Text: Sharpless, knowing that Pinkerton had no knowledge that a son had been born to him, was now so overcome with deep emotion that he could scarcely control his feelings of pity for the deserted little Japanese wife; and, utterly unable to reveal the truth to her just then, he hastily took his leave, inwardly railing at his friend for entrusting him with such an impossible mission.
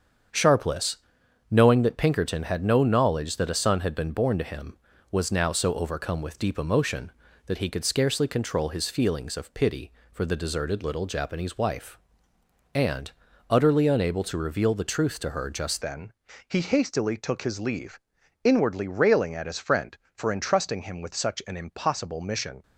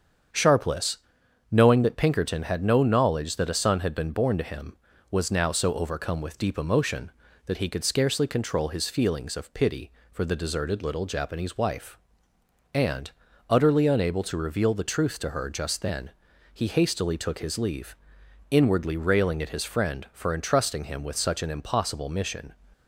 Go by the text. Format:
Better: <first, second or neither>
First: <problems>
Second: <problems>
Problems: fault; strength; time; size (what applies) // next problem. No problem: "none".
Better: second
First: starts louder than the rest; strong; until 1.8 s; 7.5 dB // changes voice at "then"; from 15.8 s on; 6.8 s long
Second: starts louder than the rest; strong; until 1.8 s; 7.5 dB